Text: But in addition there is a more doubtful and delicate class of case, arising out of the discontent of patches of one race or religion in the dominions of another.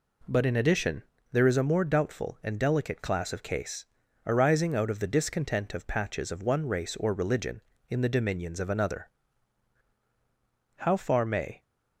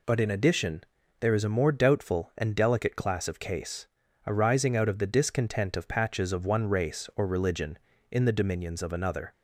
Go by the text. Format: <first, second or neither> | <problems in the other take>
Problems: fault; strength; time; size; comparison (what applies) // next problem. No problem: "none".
second | pauses between "addition" and "there"; slight; at 1.0 s; 0.30 s long; also in the second // goes on to say "How far may"; noticeable; from 10.7 s on; 0.86 s long